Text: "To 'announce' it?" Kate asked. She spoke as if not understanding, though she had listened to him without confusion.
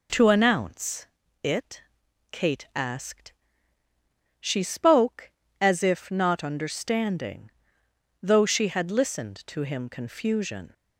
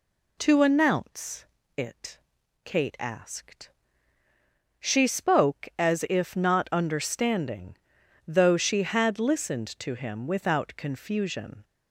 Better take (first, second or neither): second